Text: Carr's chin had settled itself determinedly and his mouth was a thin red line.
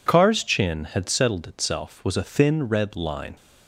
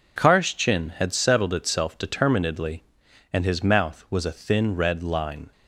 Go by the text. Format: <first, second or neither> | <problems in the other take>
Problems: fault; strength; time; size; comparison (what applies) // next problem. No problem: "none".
second | skips "determinedly and his mouth"; at 2.0 s